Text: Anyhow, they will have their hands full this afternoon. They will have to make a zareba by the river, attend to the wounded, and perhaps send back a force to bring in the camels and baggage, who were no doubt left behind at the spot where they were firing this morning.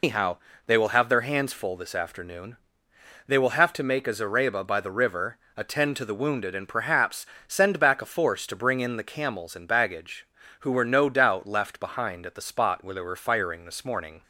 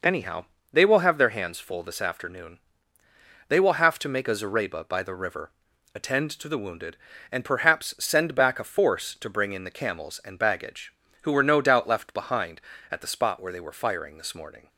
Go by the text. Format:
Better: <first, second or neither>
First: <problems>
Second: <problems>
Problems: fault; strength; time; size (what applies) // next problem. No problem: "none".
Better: second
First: loses the start of "Anyhow"; at 0.0 s; 130 ms // pauses between "perhaps" and "send"; slight; at 7.2 s; 0.20 s long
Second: none